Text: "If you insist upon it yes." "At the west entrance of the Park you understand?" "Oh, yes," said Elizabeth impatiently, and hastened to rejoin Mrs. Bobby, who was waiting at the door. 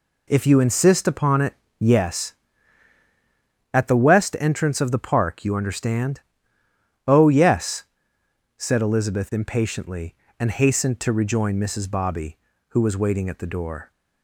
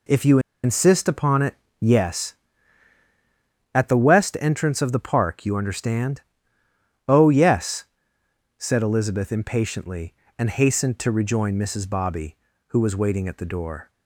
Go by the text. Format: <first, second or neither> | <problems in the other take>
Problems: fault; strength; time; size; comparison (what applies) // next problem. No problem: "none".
first | pauses between "you" and "insist"; slight; at 0.3 s; 0.24 s long // pauses between "it" and "yes"; slight; at 1.5 s; 0.24 s long; slight in the first